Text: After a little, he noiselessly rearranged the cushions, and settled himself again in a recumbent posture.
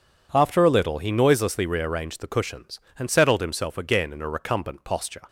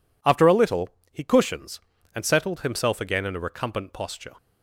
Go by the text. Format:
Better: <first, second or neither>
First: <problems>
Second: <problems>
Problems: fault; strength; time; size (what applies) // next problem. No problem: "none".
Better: first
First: none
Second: skips "noiselessly rearranged the"; at 1.2 s